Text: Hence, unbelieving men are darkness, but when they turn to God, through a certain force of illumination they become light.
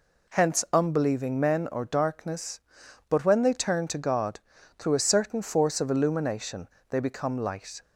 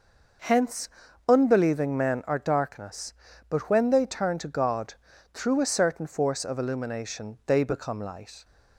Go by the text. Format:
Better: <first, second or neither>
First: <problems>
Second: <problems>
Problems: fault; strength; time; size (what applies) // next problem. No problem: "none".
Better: second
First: says "or" for "are"; at 1.6 s // pauses between "illumination" and "they"; slight; at 6.6 s; 0.22 s long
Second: none